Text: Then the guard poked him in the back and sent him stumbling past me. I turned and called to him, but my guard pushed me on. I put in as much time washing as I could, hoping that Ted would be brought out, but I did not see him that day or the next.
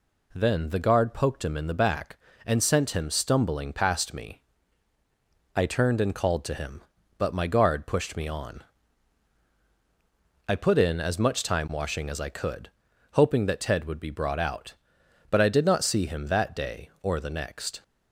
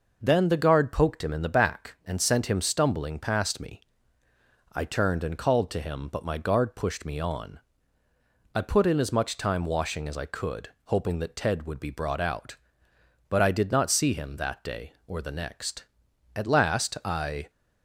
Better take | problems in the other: first | goes on to say "At last I"; noticeable; from 16.3 s on; 1.1 s long

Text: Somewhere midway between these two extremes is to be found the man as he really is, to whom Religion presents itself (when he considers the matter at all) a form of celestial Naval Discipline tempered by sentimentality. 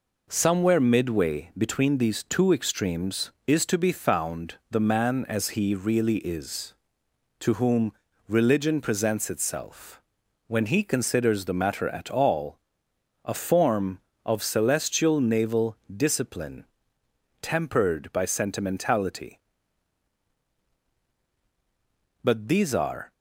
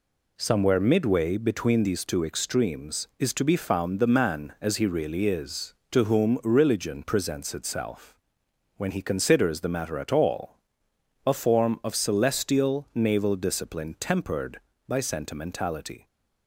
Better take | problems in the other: second | pauses between "whom" and "Religion"; slight; at 7.9 s; 0.36 s long // pauses between "Discipline" and "tempered"; noticeable; at 16.6 s; 0.74 s long // goes on to say "But these are"; noticeable; from 22.2 s on; 0.90 s long

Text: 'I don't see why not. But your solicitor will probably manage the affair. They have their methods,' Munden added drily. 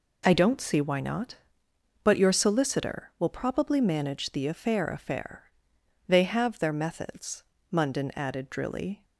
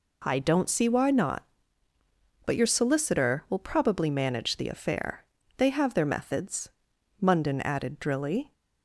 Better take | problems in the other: second | says "affair" twice; at 4.8 s

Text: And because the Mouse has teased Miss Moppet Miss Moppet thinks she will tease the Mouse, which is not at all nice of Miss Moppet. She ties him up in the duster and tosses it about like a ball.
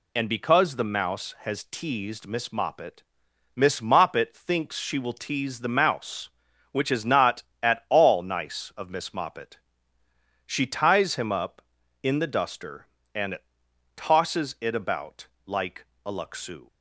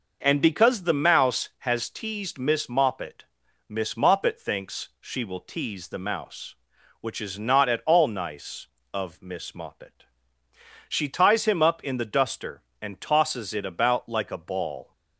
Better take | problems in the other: second | pauses between "Moppet" and "Miss"; noticeable; at 3.0 s; 0.52 s long; also in the second // pauses between "and" and "tosses"; noticeable; at 13.3 s; 0.58 s long // pauses between "about" and "like"; slight; at 15.2 s; 0.18 s long // pauses between "like" and "a"; slight; at 15.8 s; 0.20 s long // says "luxu" for "ball"; at 16.1 s

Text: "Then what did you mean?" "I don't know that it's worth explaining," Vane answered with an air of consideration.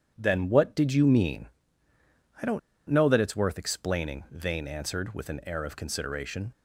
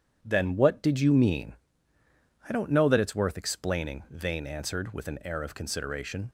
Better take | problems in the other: second | pauses between "don't" and "know"; slight; at 2.5 s; 0.29 s long

